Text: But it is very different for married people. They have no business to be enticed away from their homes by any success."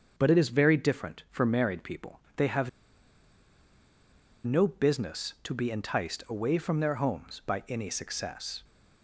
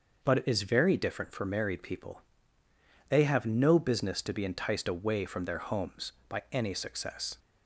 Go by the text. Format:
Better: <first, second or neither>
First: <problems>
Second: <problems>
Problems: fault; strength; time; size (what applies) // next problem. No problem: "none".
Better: second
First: starts louder than the rest; until 1.1 s; 6.5 dB // pauses between "have" and "no"; strong; at 2.6 s; 1.7 s long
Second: starts louder than the rest; until 1.2 s; 6 dB